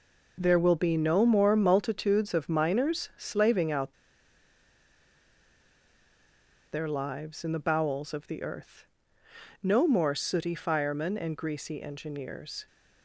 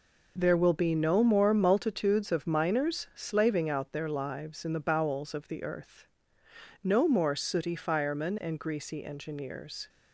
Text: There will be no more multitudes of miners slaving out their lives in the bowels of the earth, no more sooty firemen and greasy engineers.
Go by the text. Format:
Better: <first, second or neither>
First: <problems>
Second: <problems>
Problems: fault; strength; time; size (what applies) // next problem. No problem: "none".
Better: second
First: pauses between "out" and "their"; strong; at 3.9 s; 2.7 s long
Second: none